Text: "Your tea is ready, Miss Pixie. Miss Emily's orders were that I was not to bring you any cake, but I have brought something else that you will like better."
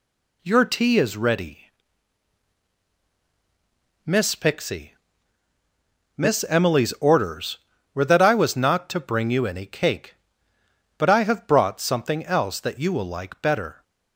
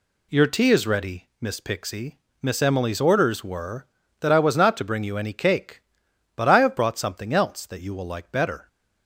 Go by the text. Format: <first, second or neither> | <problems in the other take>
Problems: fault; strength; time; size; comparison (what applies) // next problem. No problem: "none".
neither | none